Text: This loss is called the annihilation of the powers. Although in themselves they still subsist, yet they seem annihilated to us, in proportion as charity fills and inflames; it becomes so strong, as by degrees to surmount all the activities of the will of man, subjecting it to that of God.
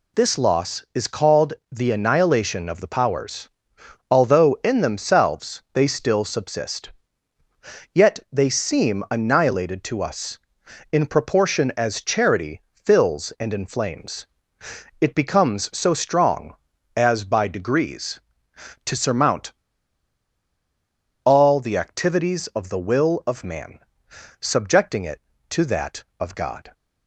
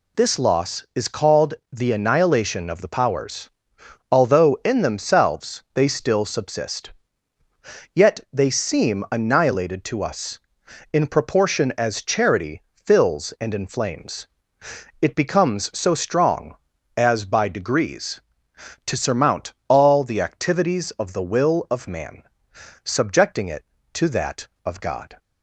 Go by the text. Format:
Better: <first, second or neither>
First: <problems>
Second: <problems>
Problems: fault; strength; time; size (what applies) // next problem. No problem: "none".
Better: second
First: pauses between "called" and "the"; slight; at 1.5 s; 0.18 s long // pauses between "surmount" and "all"; strong; at 19.5 s; 1.7 s long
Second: pauses between "called" and "the"; slight; at 1.5 s; 0.18 s long